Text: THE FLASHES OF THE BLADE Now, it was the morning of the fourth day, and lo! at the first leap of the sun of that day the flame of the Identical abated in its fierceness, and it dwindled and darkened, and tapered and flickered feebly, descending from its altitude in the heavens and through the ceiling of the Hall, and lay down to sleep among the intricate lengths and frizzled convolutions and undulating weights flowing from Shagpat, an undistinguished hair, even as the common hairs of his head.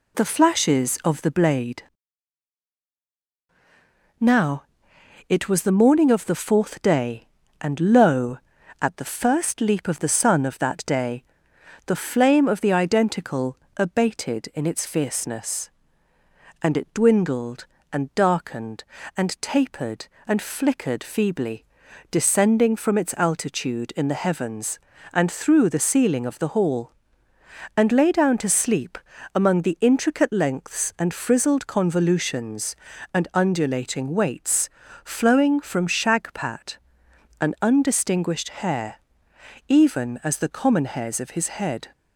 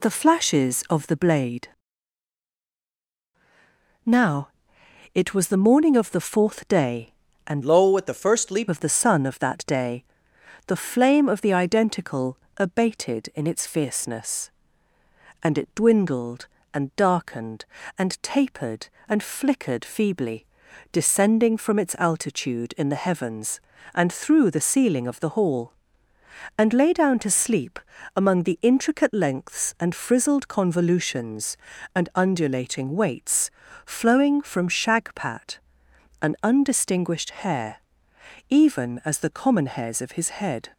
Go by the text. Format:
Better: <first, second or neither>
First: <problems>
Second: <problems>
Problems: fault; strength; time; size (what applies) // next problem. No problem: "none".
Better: first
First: pauses between "BLADE" and "Now"; strong; at 1.8 s; 2.3 s long // pauses between "day" and "the"; noticeable; at 11.2 s; 0.62 s long // pauses between "Identical" and "abated"; slight; at 13.5 s; 0.20 s long // pauses between "sleep" and "among"; at 28.9 s; 0.38 s long // pauses between "weights" and "flowing"; slight; at 34.6 s; 0.34 s long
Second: pauses between "BLADE" and "Now"; strong; at 1.6 s; 2.3 s long // changes voice from "lo" to "leap"; from 7.6 to 8.6 s; 1.0 s long // pauses between "day" and "the"; noticeable; at 10.0 s; 0.62 s long // pauses between "Identical" and "abated"; slight; at 12.3 s; 0.20 s long // pauses between "sleep" and "among"; at 27.7 s; 0.38 s long // pauses between "weights" and "flowing"; slight; at 33.5 s; 0.34 s long